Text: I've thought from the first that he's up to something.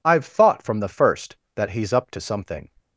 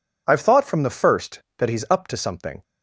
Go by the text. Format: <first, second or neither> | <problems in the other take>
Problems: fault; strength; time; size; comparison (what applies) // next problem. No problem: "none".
neither | none